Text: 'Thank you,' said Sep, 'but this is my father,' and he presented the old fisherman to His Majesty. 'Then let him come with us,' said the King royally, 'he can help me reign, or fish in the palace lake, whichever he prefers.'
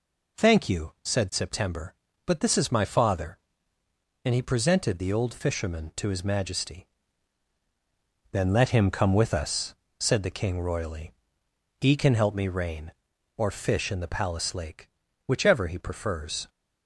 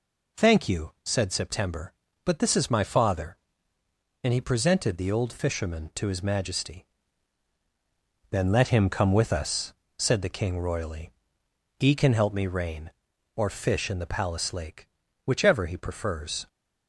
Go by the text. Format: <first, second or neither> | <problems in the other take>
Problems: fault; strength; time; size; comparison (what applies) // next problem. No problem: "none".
neither | none